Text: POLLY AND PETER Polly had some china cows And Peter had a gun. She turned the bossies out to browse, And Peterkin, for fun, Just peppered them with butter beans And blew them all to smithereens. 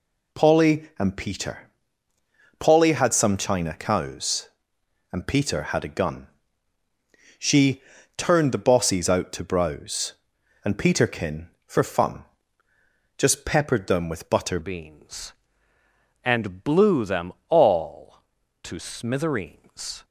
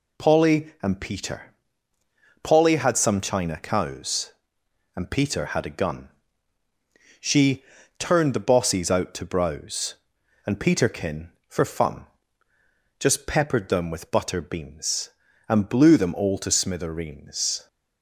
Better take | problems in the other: second | pauses between "PETER" and "Polly"; noticeable; at 1.6 s; 0.88 s long; noticeable in the second // pauses between "She" and "turned"; slight; at 7.8 s; 0.34 s long; slight in the second // changes voice at "beans"; from 14.6 s on; 5.4 s long // pauses between "them" and "all"; slight; at 17.3 s; 0.18 s long

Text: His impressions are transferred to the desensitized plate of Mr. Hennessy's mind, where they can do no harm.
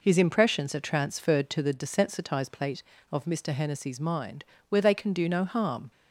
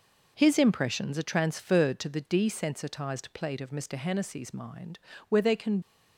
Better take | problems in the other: first | stops before "do no harm"; at 5.8 s

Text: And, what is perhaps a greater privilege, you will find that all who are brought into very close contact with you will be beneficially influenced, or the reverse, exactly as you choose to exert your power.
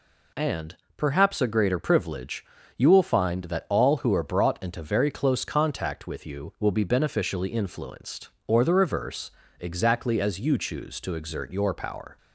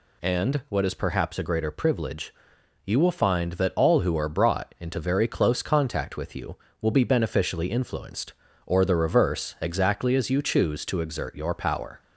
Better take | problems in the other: second | skips "what is"; at 0.8 s

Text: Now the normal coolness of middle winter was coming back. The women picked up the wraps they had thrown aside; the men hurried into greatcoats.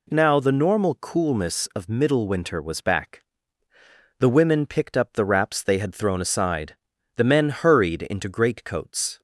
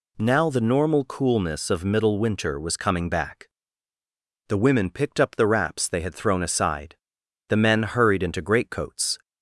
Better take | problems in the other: second | skips "coming"; at 2.8 s

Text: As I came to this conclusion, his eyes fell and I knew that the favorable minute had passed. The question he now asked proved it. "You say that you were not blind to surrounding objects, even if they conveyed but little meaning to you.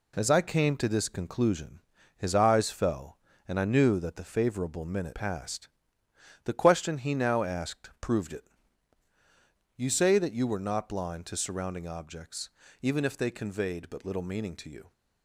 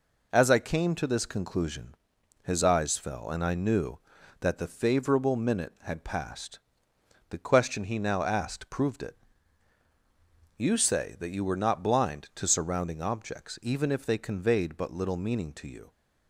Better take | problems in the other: second | skips "had"; at 5.1 s

